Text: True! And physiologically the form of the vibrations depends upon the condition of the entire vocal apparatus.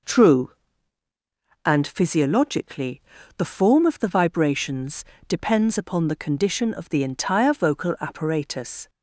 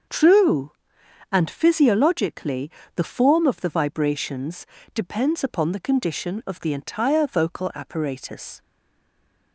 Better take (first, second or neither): first